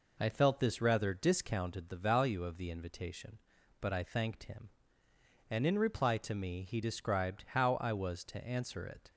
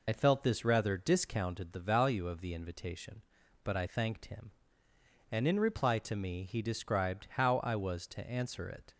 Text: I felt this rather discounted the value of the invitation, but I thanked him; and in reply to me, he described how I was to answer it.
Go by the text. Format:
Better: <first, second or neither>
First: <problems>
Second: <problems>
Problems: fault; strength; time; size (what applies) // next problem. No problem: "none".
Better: first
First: none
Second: loses the start of "I"; at 0.0 s; 50 ms